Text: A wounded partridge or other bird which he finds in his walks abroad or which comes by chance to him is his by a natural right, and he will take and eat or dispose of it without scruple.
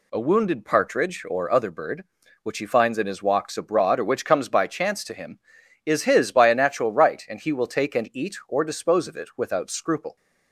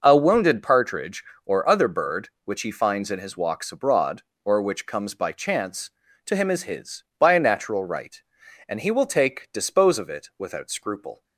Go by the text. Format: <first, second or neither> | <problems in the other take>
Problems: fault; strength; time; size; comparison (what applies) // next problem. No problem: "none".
first | skips "and eat or"; at 9.5 s